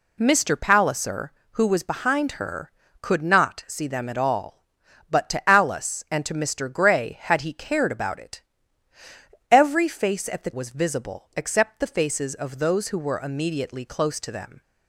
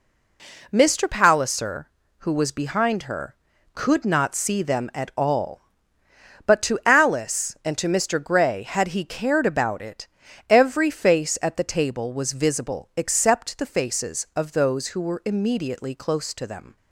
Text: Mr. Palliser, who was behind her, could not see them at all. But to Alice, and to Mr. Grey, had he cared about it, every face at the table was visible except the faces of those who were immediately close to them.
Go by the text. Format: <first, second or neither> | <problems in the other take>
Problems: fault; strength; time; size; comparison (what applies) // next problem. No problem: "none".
second | skips "table"; at 10.5 s